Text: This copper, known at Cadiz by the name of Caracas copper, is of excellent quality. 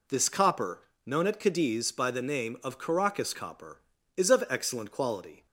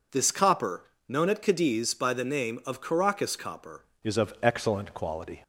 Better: first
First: none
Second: changes voice at "is"; from 4.0 s on; 1.4 s long

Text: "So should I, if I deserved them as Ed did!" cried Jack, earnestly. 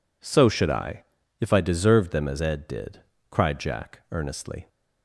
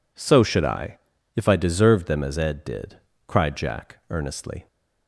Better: neither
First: none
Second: none

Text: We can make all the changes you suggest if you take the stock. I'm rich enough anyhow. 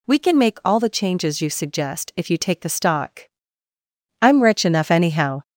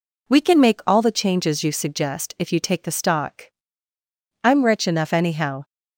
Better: second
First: gets louder; slight; throughout; 3 dB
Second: none

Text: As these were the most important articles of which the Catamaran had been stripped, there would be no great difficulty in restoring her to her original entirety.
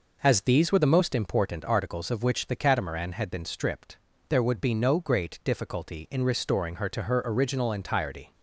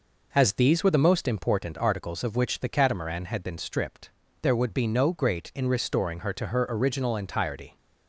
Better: first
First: none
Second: skips "difficulty"; at 5.5 s

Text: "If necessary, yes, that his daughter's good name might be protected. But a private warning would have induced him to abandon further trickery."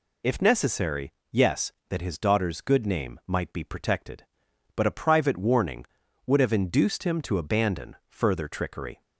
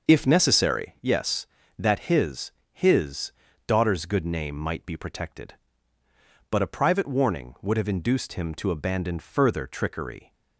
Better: first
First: none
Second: starts louder than the rest; noticeable; until 1.1 s; 6 dB // says "his" twice; at 2.7 s

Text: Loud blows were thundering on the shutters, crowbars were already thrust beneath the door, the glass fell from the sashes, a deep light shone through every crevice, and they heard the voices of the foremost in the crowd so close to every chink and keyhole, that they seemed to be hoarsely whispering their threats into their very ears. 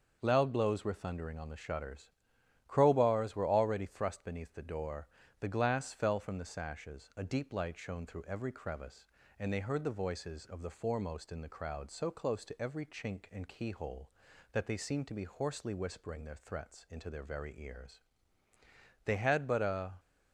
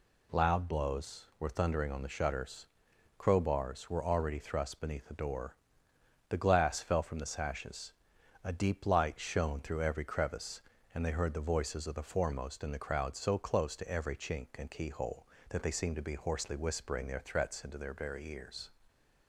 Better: second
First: starts louder than the rest; until 1.2 s; 6.5 dB // goes on to say "They had but a"; noticeable; from 19.0 s on; 0.88 s long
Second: none

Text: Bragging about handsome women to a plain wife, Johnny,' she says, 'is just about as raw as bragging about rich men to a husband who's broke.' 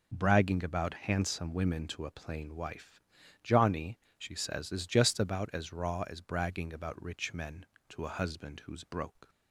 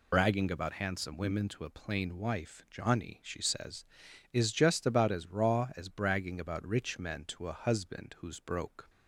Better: first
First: none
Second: loses the start of "Bragging"; at 0.1 s; 90 ms

